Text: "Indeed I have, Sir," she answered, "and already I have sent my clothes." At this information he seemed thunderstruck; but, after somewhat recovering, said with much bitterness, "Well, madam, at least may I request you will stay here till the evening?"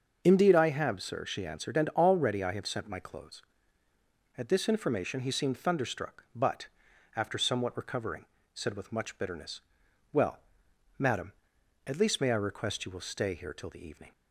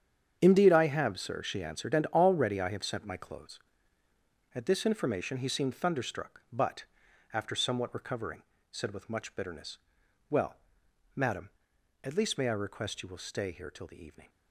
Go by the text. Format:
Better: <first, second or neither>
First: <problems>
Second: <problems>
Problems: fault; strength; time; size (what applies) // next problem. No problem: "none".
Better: first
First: starts louder than the rest; until 1.2 s; 6.5 dB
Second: gets quieter; strong; throughout; 12 dB // starts louder than the rest; strong; until 1.4 s; 8 dB